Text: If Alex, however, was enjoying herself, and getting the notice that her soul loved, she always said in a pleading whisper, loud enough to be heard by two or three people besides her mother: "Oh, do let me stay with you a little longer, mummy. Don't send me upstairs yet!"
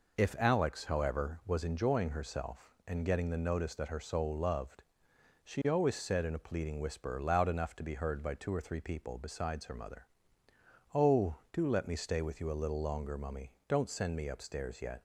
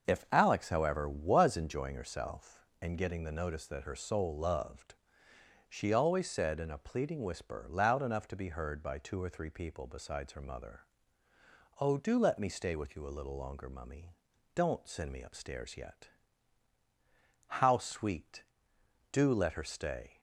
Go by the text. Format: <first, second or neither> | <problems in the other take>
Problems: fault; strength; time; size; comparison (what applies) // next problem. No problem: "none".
first | starts louder than the rest; until 1.1 s; 6.5 dB // goes on to say "How sweet Do let her stay"; strong; from 17.4 s on; 2.7 s long